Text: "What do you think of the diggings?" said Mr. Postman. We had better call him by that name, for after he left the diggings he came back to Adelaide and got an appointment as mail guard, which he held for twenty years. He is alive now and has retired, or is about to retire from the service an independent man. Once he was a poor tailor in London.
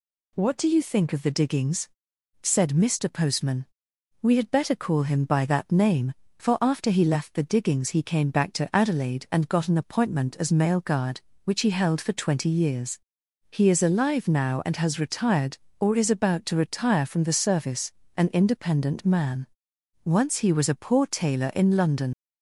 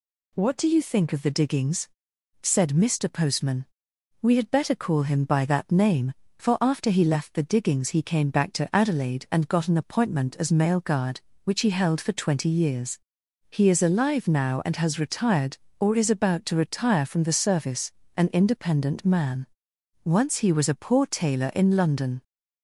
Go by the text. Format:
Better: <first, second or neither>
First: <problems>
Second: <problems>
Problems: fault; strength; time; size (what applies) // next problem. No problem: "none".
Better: second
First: pauses between "service" and "an"; slight; at 17.9 s; 0.26 s long // leaves "London" unfinished; at 22.1 s; 95 ms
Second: pauses between "service" and "an"; slight; at 17.9 s; 0.26 s long